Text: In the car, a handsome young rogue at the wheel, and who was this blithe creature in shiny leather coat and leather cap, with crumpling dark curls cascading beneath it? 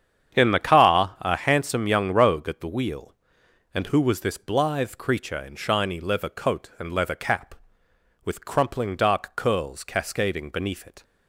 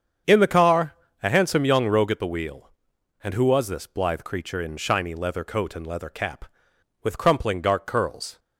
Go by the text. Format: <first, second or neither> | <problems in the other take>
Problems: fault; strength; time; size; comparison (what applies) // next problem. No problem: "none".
first | starts louder than the rest; strong; until 1.5 s; 7.5 dB; strong in the first // stops before "cascading beneath it"; at 8.3 s